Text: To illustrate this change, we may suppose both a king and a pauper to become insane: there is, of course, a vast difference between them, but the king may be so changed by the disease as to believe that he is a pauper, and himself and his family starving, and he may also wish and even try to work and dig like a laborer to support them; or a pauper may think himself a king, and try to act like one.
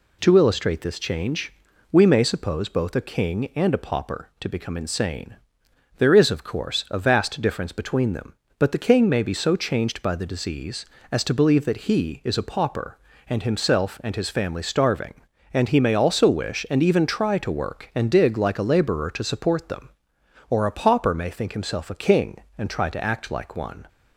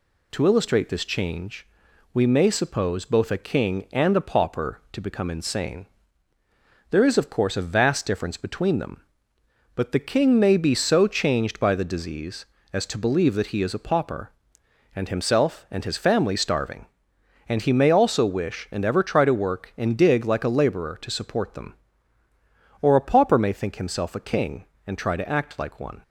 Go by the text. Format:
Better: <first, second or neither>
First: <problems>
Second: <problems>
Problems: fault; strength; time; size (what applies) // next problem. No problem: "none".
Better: first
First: none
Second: says "ever" for "even"; at 18.8 s